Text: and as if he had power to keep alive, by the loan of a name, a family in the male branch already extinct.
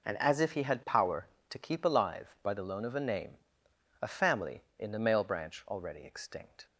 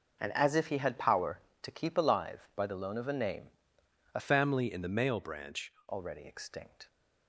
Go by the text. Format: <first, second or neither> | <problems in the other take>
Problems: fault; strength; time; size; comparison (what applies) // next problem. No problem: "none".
first | changes voice from "family" to "branch"; from 4.1 to 5.7 s; 1.6 s long